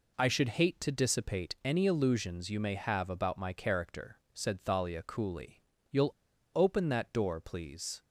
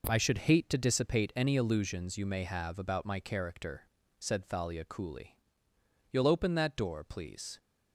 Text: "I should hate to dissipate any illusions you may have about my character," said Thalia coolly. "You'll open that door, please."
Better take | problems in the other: second | pauses between "You'll" and "open"; at 6.1 s; 0.42 s long

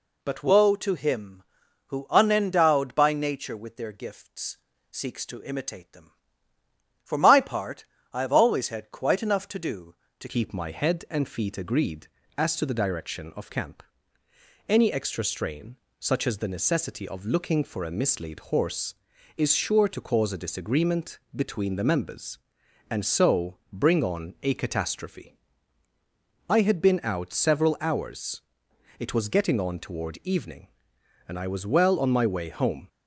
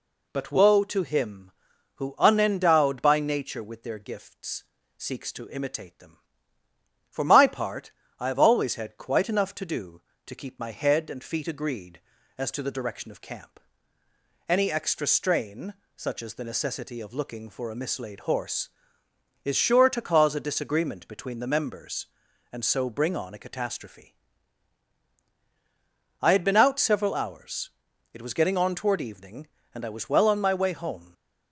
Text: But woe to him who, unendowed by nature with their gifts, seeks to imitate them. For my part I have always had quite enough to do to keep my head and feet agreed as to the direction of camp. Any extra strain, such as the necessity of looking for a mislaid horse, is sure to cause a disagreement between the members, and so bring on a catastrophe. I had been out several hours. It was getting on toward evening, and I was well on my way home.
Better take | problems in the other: second | pauses between "part" and "I"; slight; at 7.8 s; 0.28 s long; slight in the second // changes voice at "keep"; from 10.2 s on; 22.6 s long // pauses between "disagreement" and "between"; slight; at 21.1 s; 0.16 s long

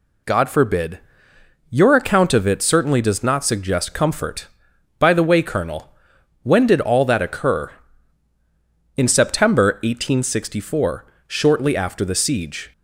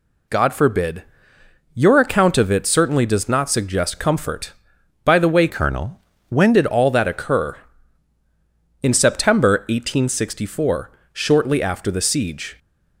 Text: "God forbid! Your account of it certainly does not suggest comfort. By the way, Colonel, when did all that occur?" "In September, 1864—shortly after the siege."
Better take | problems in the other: first | changes voice from "Colonel" to "when"; from 5.4 to 6.5 s; 1.1 s long

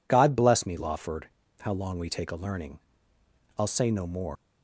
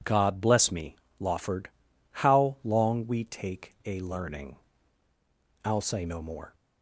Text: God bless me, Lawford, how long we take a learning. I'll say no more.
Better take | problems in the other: second | leaves "more" unfinished; at 4.3 s; 115 ms

